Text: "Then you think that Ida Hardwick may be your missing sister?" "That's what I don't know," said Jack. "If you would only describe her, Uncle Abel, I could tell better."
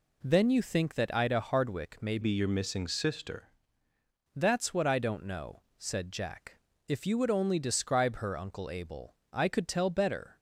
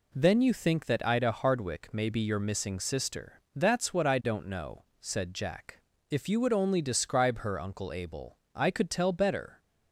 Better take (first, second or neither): second